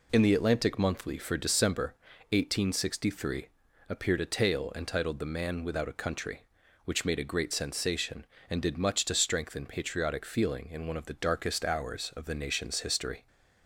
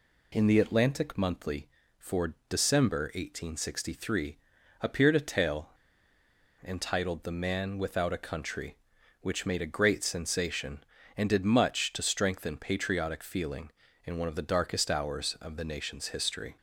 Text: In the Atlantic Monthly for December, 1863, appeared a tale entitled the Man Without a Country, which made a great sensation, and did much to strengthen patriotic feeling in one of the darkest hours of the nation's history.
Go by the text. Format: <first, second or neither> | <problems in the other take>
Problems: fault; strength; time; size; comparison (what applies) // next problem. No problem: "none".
first | pauses between "for" and "December"; slight; at 2.3 s; 0.16 s long // pauses between "tale" and "entitled"; noticeable; at 5.6 s; 0.97 s long